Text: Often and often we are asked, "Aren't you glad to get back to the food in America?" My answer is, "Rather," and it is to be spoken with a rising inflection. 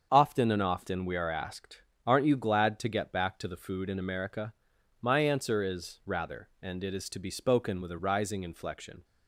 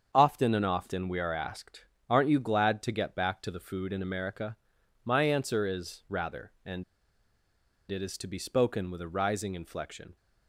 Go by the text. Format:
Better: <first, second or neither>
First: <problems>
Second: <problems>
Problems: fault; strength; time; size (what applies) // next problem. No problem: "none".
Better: first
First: starts louder than the rest; strong; until 1.1 s; 7 dB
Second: starts louder than the rest; strong; until 1.1 s; 7 dB // pauses between "and" and "it"; at 6.8 s; 1.0 s long